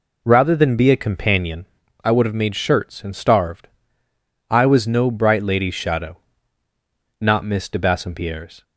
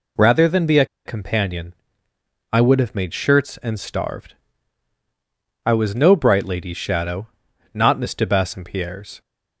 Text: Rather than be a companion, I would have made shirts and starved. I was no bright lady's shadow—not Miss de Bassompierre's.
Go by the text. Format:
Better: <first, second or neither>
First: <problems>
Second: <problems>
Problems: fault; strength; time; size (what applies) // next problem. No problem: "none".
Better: first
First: none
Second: pauses between "a" and "companion"; slight; at 0.8 s; 0.20 s long